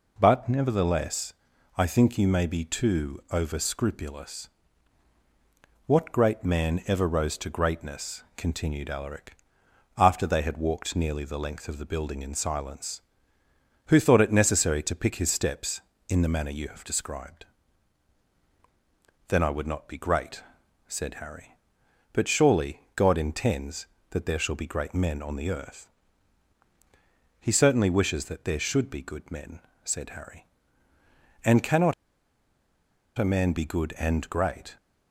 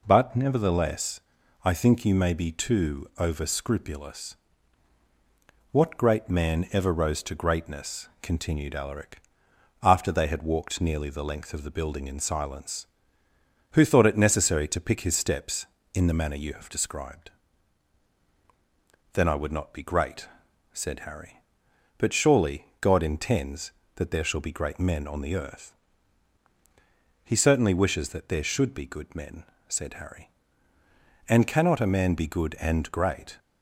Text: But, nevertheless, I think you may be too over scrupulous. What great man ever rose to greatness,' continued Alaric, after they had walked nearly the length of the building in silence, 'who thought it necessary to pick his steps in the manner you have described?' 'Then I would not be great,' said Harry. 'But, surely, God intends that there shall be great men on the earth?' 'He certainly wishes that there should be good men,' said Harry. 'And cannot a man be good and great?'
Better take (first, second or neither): second